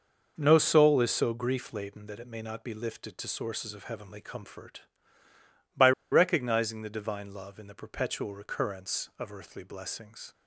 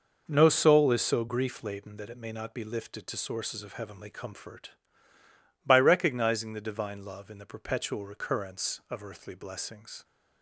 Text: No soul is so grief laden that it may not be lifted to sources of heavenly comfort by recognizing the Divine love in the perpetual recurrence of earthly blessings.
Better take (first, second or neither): second